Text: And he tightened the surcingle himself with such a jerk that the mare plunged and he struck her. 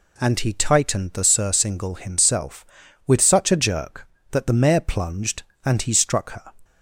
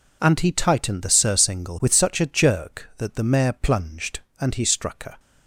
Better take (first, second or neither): first